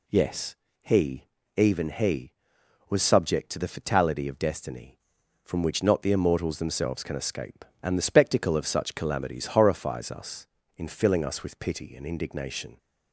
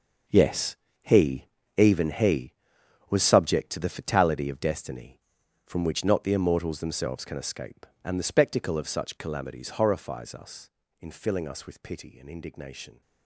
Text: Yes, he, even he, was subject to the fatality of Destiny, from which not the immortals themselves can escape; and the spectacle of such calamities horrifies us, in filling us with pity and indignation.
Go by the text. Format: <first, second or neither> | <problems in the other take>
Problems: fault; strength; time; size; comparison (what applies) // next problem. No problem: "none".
first | gets quieter; strong; throughout; 12.5 dB